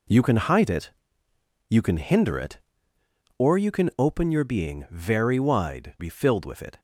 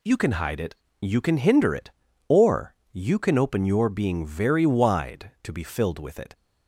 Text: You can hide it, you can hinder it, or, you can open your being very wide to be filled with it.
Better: second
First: skips "to"; at 5.9 s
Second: none

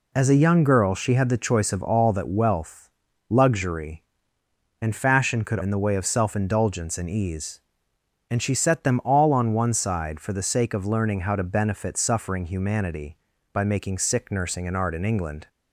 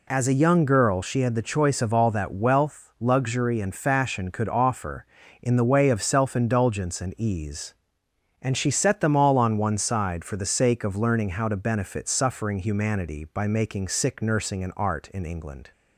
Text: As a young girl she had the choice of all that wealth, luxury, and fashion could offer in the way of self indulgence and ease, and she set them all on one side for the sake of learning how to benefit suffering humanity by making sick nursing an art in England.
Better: second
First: skips "offer"; at 5.5 s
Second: none

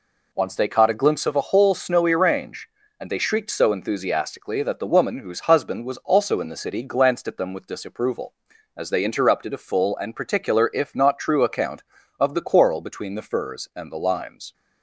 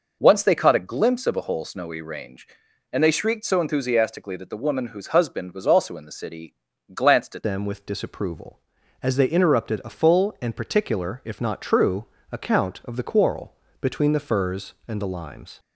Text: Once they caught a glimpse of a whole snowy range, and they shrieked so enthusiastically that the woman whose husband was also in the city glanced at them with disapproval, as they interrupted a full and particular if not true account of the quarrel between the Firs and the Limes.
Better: first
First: none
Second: pauses between "city" and "glanced"; at 6.5 s; 0.40 s long // changes voice at "them"; from 7.4 s on; 8.1 s long // pauses between "true" and "account"; slight; at 12.0 s; 0.26 s long // pauses between "quarrel" and "between"; slight; at 13.5 s; 0.28 s long

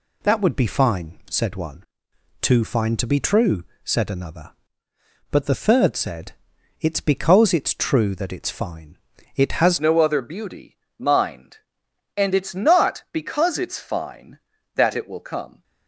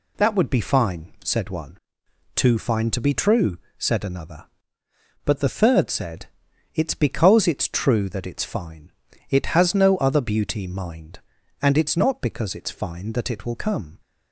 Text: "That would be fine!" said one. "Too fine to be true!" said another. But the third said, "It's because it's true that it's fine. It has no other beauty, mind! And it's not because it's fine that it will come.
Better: second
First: changes voice at "no"; from 9.8 s on; 5.8 s long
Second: none

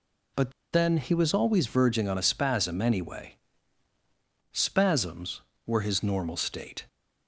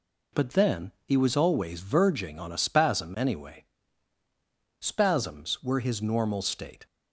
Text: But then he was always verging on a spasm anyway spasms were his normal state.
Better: second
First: pauses between "But" and "then"; slight; at 0.4 s; 0.22 s long // pauses between "anyway" and "spasms"; at 3.3 s; 1.2 s long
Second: pauses between "anyway" and "spasms"; at 3.6 s; 1.1 s long

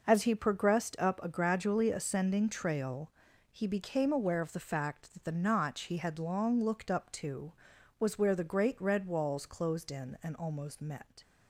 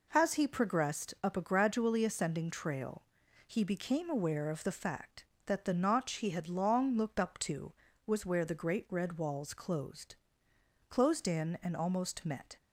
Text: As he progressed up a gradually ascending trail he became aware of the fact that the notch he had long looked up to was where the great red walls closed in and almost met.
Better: first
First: pauses between "trail" and "he"; at 3.1 s; 0.44 s long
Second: pauses between "trail" and "he"; noticeable; at 3.0 s; 0.46 s long // says "closed" twice; at 10.8 s

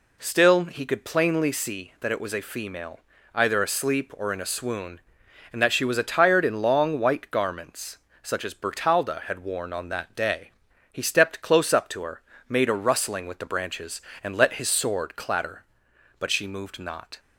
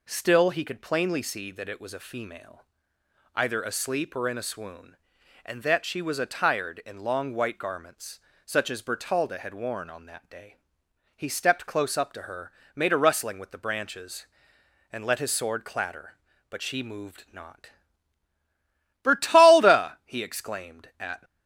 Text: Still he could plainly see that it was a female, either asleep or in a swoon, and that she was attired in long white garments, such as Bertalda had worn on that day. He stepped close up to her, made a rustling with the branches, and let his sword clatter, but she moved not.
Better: first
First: none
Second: goes on to say "Bertalda he exclaimed at"; strong; from 19.0 s on; 2.2 s long

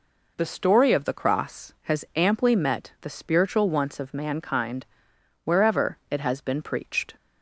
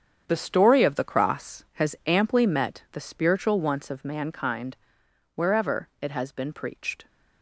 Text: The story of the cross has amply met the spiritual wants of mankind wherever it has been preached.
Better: first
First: pauses between "mankind" and "wherever"; noticeable; at 4.8 s; 0.60 s long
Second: gets quieter; strong; throughout; 10.5 dB // pauses between "mankind" and "wherever"; noticeable; at 4.7 s; 0.60 s long

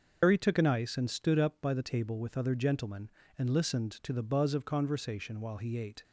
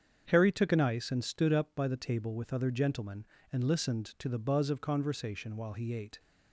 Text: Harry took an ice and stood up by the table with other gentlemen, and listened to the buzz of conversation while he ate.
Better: second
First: loses the start of "Harry"; at 0.2 s; 100 ms // starts louder than the rest; until 1.2 s; 6 dB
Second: starts louder than the rest; strong; until 1.3 s; 7.5 dB

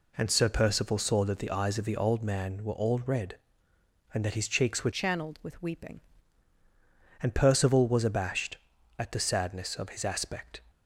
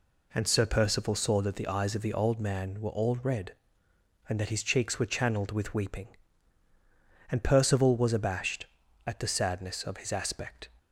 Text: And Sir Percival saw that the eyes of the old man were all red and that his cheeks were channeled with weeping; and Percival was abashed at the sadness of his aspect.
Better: second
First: changes voice from "channeled" to "weeping"; from 4.9 to 6.0 s; 1.1 s long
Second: none

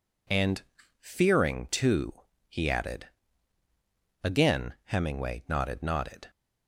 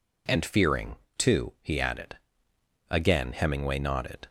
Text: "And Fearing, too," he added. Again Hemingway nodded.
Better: second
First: pauses between "And" and "Fearing"; at 0.6 s; 0.38 s long // says "nodded" twice; at 5.8 s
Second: none

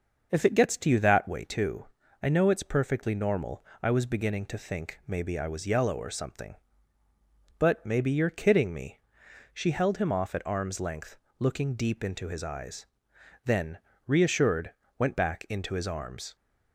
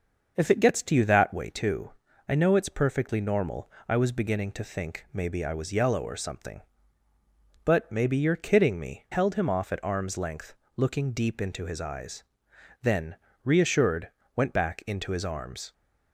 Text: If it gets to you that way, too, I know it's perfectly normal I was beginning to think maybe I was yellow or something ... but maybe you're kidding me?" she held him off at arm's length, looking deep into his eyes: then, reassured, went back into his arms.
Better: first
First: starts louder than the rest; until 1.3 s; 6 dB // pauses between "normal" and "I"; slight; at 3.6 s; 0.16 s long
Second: starts louder than the rest; until 1.3 s; 6 dB // pauses between "normal" and "I"; slight; at 3.7 s; 0.16 s long // skips "she"; at 9.0 s

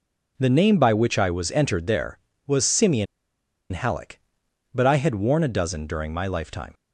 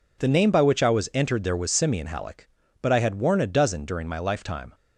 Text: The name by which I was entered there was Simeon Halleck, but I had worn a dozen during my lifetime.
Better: second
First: pauses between "Simeon" and "Halleck"; noticeable; at 3.0 s; 0.65 s long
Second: none

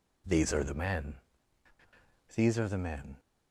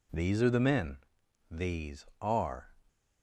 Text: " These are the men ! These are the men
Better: first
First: none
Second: stops before "the men"; at 2.8 s

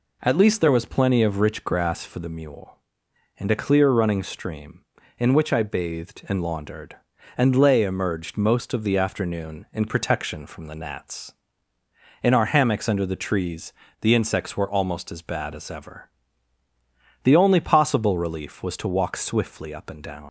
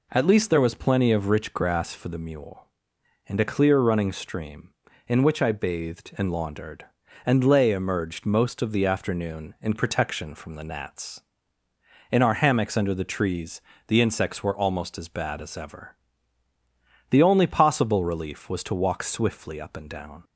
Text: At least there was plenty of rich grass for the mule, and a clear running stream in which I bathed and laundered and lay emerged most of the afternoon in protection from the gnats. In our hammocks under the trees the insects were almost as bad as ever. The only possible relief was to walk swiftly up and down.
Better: second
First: pauses between "trees" and "the"; slight; at 13.7 s; 0.29 s long // leaves "down" unfinished; at 20.2 s; 80 ms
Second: pauses between "trees" and "the"; slight; at 13.5 s; 0.28 s long

